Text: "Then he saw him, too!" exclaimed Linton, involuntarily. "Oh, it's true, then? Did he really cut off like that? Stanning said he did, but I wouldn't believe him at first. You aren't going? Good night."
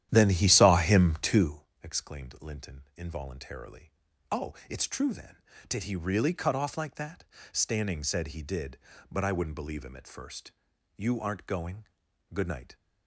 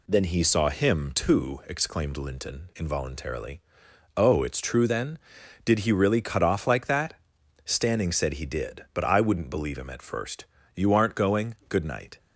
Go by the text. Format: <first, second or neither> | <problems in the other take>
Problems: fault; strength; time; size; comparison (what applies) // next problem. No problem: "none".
second | starts louder than the rest; strong; until 1.7 s; 11.5 dB